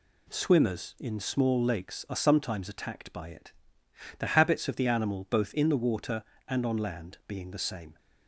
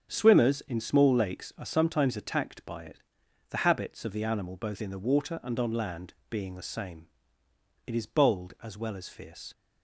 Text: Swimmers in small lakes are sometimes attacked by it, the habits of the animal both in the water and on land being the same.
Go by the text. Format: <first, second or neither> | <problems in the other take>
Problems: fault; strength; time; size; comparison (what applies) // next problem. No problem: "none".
first | starts louder than the rest; strong; until 1.1 s; 7.5 dB // pauses between "land" and "being"; slight; at 6.1 s; 0.16 s long // goes on to say "It is bold as well as fierce"; from 7.8 s on; 1.6 s long